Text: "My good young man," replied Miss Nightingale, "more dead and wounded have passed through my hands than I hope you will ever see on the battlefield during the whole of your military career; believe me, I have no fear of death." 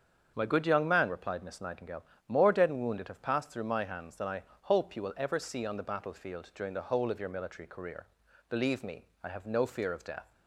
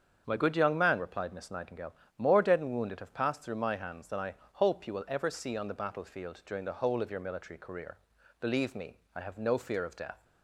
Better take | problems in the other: neither | starts louder than the rest; strong; the same in both // pauses between "I" and "hope"; slight; the same in both

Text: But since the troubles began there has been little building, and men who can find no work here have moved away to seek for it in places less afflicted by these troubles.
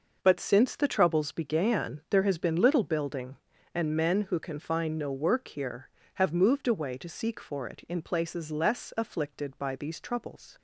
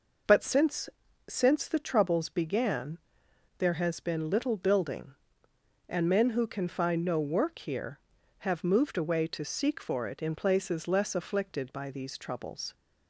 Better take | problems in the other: first | says "since" twice; at 1.2 s // pauses between "began" and "there"; noticeable; at 2.9 s; 0.60 s long

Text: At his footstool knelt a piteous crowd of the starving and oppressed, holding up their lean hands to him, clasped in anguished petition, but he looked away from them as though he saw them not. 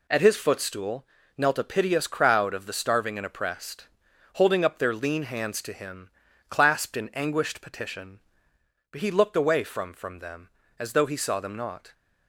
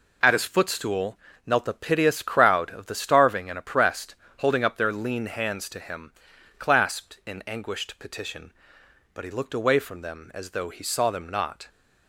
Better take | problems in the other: second | pauses between "footstool" and "knelt"; slight; at 1.0 s; 0.30 s long; slight in the second // says "from" twice; at 9.9 s

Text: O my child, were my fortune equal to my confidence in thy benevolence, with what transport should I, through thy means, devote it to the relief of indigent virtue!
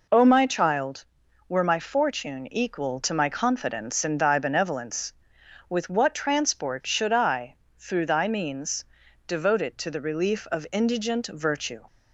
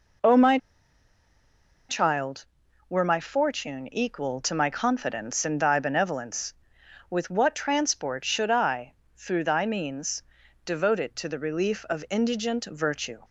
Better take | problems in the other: first | pauses between "my" and "child"; strong; at 0.5 s; 1.3 s long

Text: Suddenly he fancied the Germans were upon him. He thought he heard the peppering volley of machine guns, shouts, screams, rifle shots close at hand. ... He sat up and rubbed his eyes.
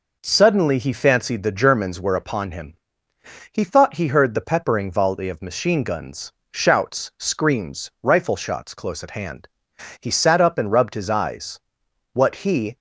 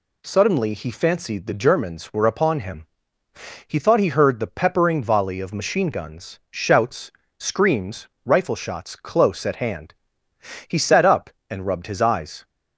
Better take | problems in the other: second | goes on to say "What he"; noticeable; from 12.1 s on; 0.62 s long

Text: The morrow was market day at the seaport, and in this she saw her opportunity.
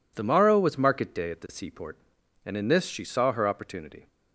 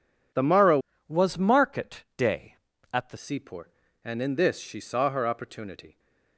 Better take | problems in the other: first | changes voice from "was" to "the"; from 1.0 to 3.1 s; 2.1 s long

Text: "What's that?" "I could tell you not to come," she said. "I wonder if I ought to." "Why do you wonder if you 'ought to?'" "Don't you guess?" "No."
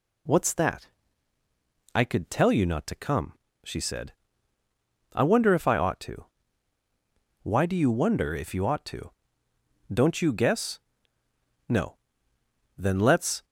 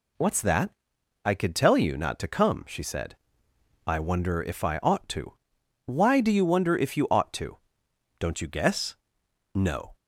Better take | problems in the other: second | goes on to say "Then let's"; noticeable; from 12.7 s on; 0.68 s long

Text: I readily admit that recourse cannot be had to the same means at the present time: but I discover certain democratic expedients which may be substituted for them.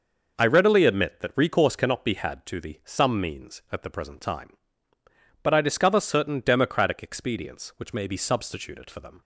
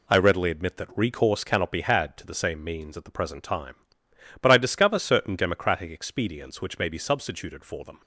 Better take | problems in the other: second | says "some" for "same"; at 2.8 s

